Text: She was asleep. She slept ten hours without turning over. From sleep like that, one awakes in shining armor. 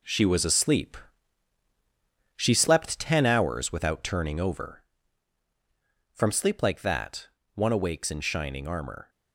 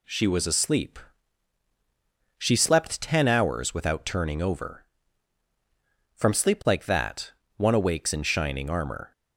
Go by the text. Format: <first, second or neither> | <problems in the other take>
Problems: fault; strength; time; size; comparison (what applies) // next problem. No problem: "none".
second | gets quieter; strong; throughout; 9 dB